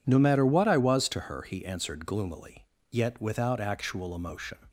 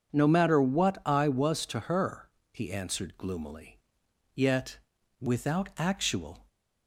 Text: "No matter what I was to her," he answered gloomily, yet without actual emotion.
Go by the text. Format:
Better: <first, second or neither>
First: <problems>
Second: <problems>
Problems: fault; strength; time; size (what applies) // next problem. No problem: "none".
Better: first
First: none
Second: starts louder than the rest; until 1.1 s; 7 dB // pauses between "yet" and "without"; at 4.7 s; 0.42 s long // stops before "emotion"; at 6.4 s